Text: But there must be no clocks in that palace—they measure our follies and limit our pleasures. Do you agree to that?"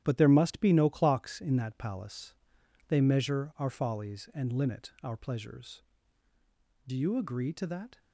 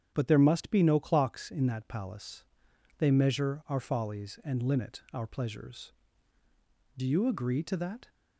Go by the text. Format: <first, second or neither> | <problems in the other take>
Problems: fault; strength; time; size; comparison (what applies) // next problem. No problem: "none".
second | gets quieter; strong; throughout; 8 dB // starts louder than the rest; strong; until 1.0 s; 11 dB; strong in the second